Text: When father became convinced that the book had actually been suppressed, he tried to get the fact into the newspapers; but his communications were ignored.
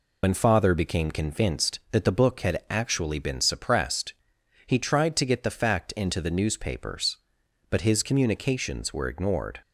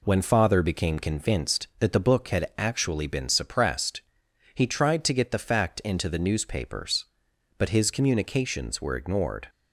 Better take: second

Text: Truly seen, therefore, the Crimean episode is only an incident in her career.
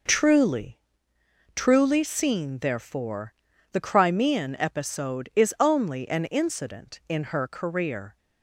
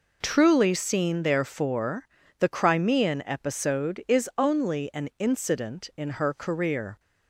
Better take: second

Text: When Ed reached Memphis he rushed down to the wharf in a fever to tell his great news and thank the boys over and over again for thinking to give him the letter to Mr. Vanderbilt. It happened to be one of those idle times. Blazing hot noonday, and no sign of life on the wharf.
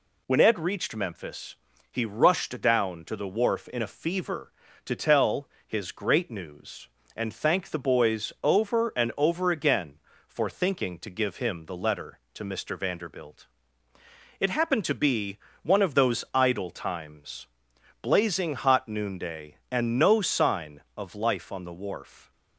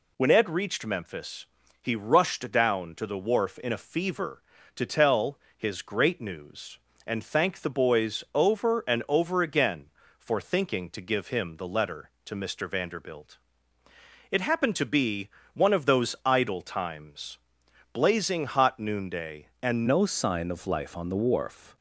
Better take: first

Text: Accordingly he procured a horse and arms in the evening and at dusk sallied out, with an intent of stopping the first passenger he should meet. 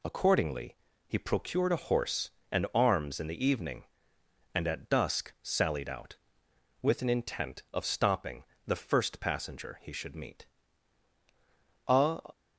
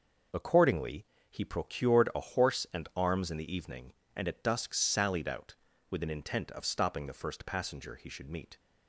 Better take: second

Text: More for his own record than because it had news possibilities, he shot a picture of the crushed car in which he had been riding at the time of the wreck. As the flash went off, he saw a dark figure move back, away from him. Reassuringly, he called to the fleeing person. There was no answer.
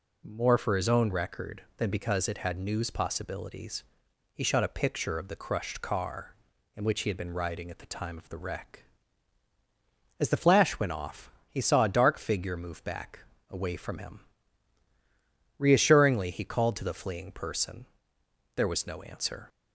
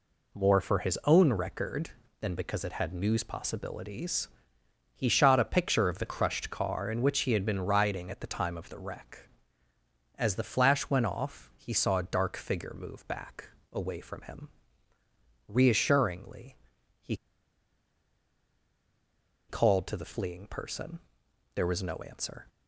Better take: first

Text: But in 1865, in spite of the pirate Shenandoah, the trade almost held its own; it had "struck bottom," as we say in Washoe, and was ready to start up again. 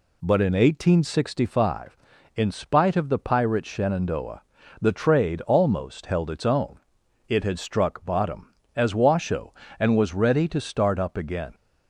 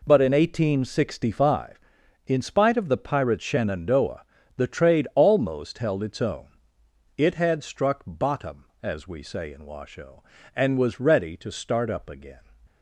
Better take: second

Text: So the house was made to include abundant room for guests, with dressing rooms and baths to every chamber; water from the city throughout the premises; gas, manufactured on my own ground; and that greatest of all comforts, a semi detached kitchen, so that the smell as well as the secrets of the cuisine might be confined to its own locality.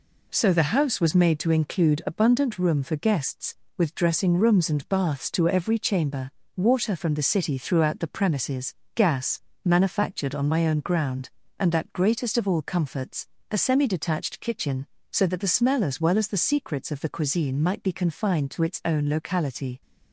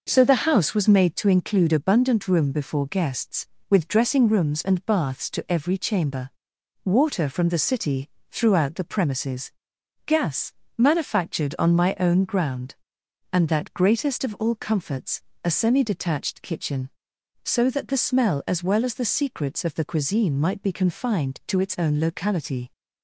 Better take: first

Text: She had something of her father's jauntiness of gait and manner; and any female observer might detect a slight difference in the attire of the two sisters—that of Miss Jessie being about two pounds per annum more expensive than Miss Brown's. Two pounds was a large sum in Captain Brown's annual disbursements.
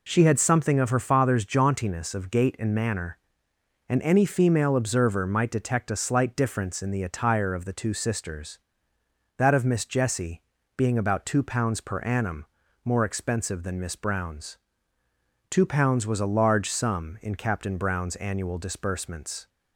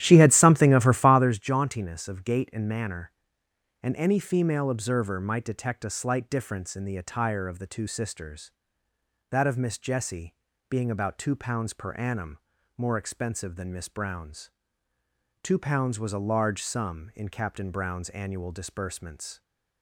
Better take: first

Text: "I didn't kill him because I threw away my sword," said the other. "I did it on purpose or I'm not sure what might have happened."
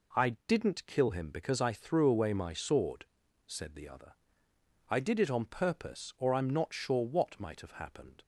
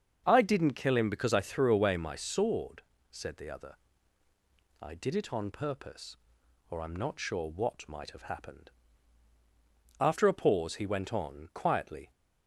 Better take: first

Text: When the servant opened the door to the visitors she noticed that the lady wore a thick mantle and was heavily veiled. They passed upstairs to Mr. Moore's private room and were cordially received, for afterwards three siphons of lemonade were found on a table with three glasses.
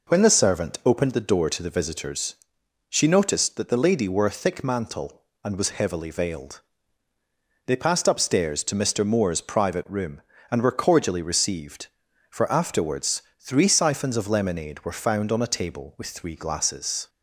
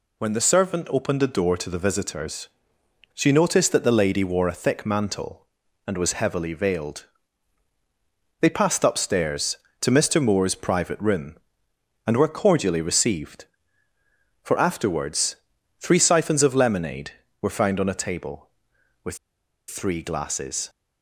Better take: first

